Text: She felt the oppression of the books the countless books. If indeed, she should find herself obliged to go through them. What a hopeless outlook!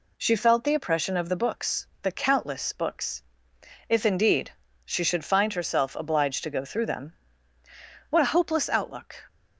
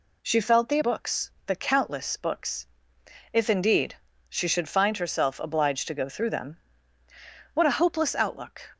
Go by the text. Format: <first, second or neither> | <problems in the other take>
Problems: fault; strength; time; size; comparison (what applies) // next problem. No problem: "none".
first | skips "oppression of the"; at 0.8 s // pauses between "books" and "the"; slight; at 1.3 s; 0.16 s long; slight in the first